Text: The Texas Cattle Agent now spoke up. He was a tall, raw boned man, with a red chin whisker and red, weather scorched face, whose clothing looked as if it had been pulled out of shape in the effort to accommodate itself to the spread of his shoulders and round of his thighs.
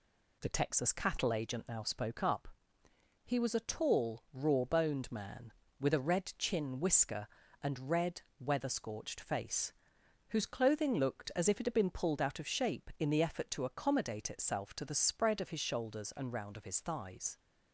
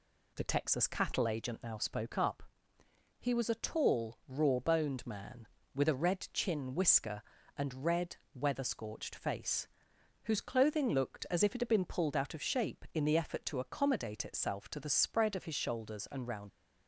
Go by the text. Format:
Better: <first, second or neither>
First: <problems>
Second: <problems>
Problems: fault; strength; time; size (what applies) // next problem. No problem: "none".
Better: first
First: none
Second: stops before "of his thighs"; at 16.4 s